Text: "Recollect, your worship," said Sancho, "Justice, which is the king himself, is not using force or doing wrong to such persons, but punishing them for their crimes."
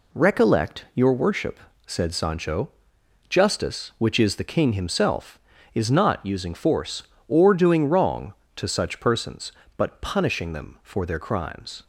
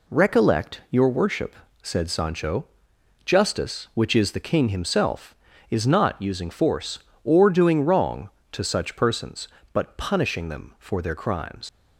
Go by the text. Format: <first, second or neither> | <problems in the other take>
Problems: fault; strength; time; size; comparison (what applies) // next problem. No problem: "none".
first | leaves "crimes" unfinished; at 11.6 s; 100 ms